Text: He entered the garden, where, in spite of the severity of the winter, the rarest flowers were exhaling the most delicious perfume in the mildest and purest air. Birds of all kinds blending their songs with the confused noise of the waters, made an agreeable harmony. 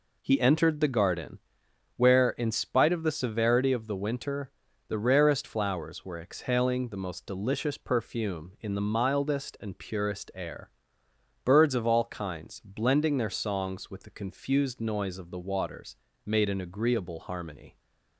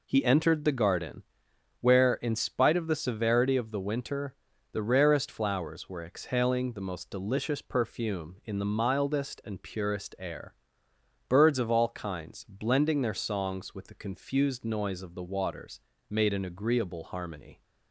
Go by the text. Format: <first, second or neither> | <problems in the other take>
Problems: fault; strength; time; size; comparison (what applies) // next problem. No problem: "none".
neither | none